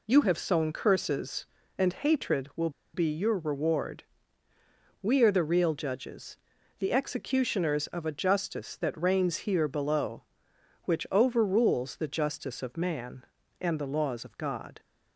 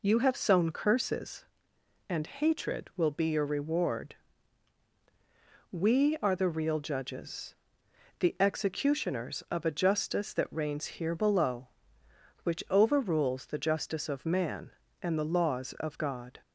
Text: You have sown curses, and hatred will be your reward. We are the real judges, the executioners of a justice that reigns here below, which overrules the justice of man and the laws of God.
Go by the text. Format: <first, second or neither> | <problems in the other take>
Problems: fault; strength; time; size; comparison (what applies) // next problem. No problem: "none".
second | pauses between "will" and "be"; slight; at 2.7 s; 0.23 s long